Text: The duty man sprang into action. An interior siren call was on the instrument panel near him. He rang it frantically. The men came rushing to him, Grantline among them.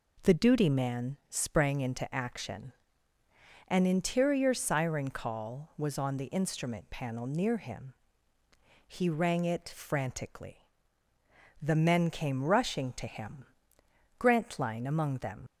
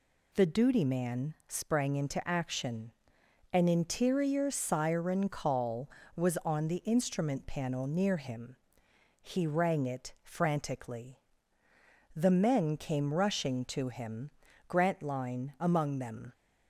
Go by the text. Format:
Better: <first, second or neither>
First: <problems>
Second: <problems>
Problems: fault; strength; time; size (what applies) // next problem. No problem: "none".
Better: second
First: leaves "them" unfinished; at 15.4 s; 60 ms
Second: none